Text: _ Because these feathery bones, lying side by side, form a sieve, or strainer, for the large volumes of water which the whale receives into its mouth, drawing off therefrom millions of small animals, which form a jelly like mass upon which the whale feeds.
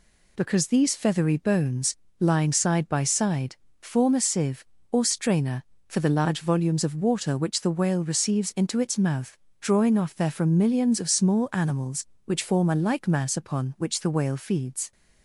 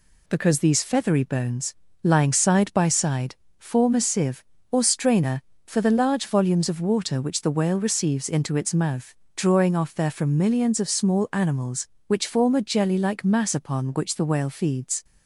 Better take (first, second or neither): second